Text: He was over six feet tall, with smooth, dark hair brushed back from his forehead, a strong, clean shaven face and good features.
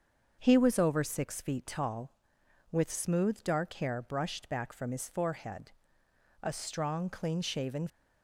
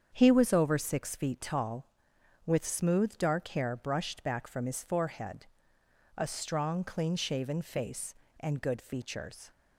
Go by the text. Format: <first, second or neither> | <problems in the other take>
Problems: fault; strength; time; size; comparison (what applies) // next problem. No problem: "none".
second | starts louder than the rest; until 1.4 s; 6.5 dB; strong in the second // stops before "face and good features"; at 7.8 s